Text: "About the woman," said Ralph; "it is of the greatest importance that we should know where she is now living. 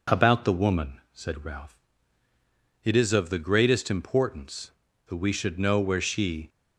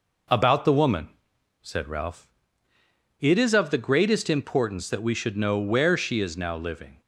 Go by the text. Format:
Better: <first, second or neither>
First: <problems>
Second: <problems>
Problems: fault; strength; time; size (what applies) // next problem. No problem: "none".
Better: second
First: stops before "is now living"; at 6.4 s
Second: none